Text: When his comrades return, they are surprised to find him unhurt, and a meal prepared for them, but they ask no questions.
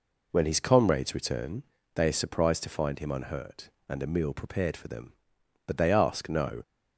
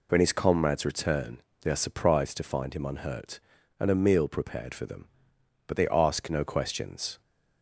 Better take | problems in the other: second | stops before "questions"; at 6.6 s

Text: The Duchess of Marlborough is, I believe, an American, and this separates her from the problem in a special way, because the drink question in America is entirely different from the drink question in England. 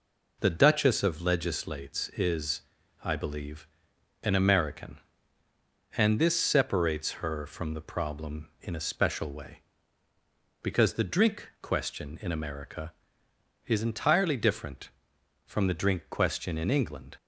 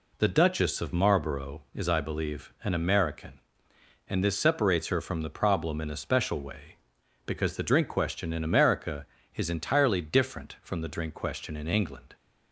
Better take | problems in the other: second | says "Legislates" for "Marlborough"; at 1.2 s

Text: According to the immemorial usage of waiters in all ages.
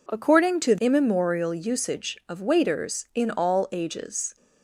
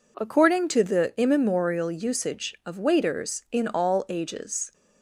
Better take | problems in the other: second | skips "the"; at 0.7 s

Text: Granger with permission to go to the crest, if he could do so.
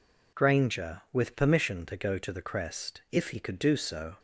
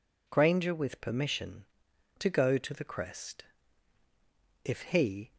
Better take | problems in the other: first | stops before "could do so"; at 5.3 s

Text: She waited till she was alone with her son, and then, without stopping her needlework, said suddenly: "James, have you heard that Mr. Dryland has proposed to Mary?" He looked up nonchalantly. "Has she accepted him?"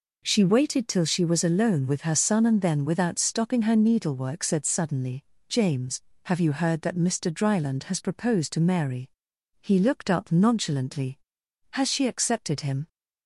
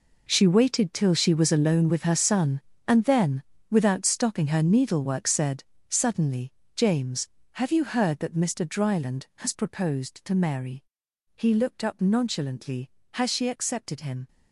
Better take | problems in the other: first | gets quieter; strong; throughout; 14 dB // pauses between "said" and "suddenly"; slight; at 5.6 s; 0.24 s long

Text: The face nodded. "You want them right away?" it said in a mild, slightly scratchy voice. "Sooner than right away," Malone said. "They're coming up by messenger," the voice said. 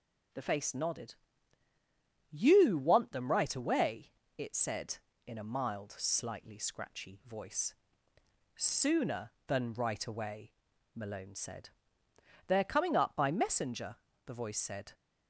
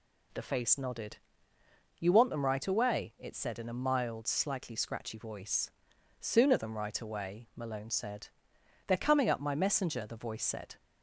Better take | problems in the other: first | says "my" for "by"; at 9.4 s

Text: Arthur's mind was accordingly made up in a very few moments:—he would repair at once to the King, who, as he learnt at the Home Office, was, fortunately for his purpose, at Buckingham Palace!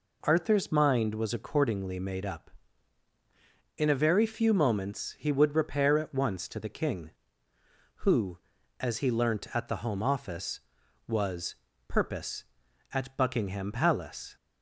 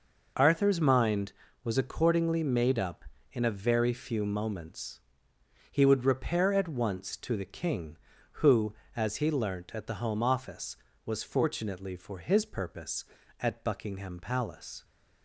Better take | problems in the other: second | skips "fortunately for his"; at 11.7 s

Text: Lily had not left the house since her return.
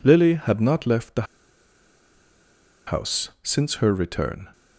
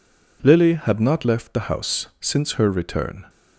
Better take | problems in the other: second | pauses between "the" and "house"; strong; at 1.2 s; 1.6 s long

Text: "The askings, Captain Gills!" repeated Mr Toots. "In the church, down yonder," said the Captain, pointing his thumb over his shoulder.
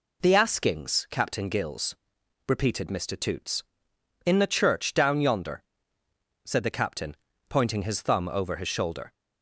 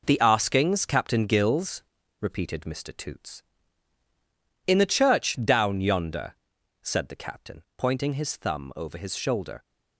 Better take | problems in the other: first | gets quieter; strong; throughout; 7.5 dB

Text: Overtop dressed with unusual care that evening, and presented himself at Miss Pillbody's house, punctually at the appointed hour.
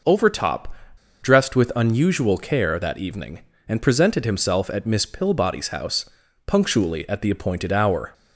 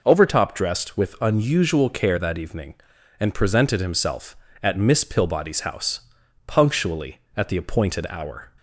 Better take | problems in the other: second | pauses between "Overtop" and "dressed"; noticeable; at 0.7 s; 0.48 s long

